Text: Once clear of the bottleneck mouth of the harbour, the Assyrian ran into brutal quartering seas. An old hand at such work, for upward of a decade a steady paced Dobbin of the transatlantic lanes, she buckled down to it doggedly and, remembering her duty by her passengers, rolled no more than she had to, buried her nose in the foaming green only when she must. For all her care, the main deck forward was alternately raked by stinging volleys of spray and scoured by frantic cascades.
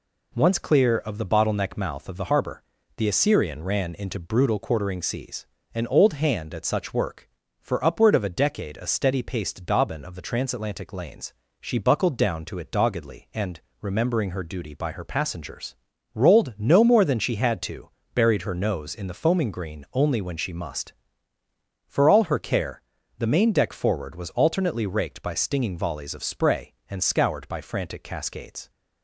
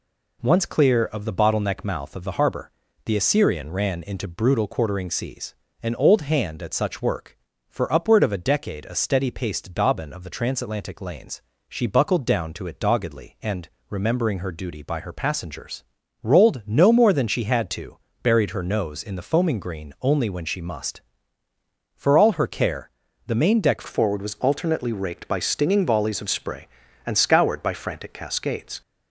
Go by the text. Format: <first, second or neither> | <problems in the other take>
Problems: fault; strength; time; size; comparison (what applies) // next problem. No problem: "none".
first | changes voice at "forward"; from 23.8 s on; 5.0 s long